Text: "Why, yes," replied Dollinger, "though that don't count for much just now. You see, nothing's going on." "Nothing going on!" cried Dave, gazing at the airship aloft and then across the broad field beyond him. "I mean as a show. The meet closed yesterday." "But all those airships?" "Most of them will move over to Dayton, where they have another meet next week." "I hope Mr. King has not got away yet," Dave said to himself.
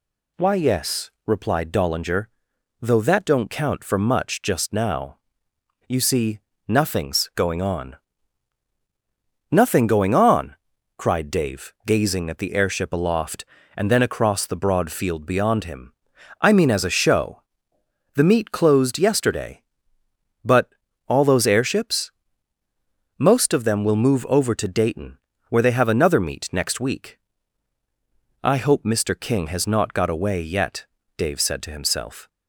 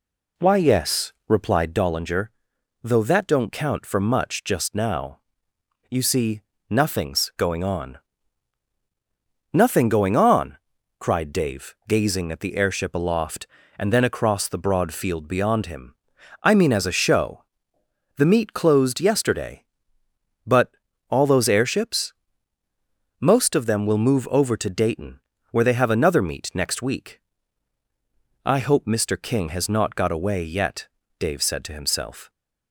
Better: first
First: pauses between "But" and "all"; slight; at 20.7 s; 0.36 s long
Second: starts louder than the rest; slight; until 1.8 s; 2.5 dB // pauses between "But" and "all"; slight; at 20.7 s; 0.36 s long

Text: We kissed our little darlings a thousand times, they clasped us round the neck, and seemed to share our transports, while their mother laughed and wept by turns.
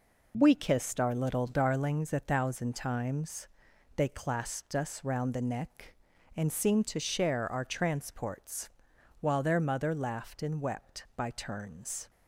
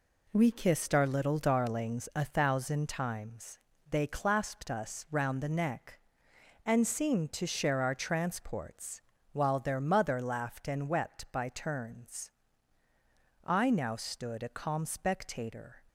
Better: first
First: none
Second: goes on to say "I now stood a calm spectator"; strong; from 13.4 s on; 2.3 s long

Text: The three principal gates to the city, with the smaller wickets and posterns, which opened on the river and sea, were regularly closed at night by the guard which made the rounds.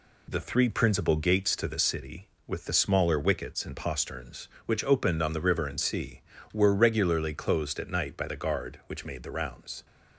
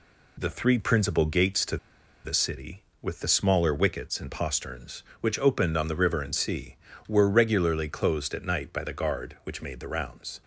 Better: first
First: none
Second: pauses between "to" and "the"; noticeable; at 1.7 s; 0.48 s long

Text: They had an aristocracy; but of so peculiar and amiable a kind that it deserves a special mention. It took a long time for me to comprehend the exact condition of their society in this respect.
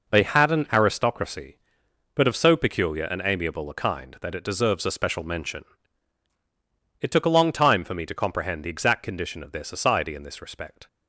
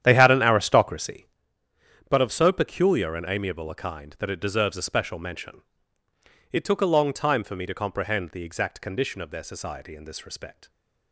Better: first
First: none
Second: starts louder than the rest; strong; until 1.4 s; 10 dB

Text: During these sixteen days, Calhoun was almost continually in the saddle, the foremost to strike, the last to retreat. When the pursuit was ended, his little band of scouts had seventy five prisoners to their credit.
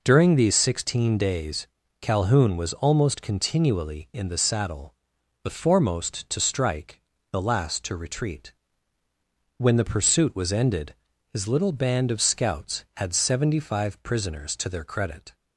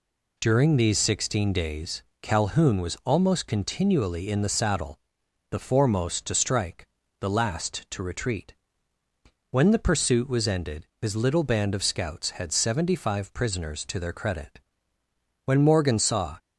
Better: first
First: none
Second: goes on to say "When Morgan saw"; noticeable; from 15.4 s on; 0.92 s long

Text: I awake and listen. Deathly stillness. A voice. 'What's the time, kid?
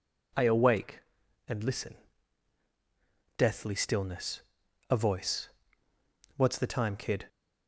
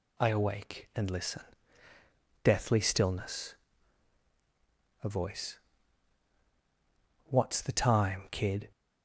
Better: neither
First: none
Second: none

